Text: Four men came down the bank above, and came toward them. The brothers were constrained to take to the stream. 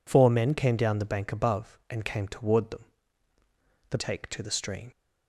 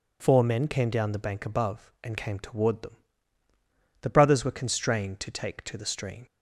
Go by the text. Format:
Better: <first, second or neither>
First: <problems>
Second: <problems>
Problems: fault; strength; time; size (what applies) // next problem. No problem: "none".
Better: second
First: skips "brothers were constrained to"; at 3.9 s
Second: none